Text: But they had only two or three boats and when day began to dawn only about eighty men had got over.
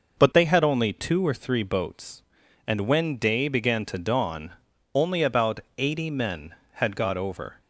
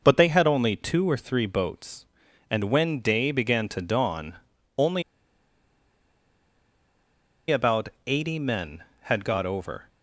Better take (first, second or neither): first